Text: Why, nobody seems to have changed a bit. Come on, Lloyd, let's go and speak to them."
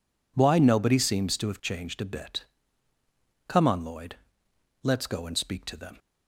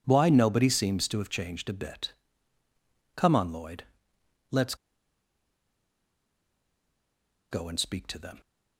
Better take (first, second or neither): first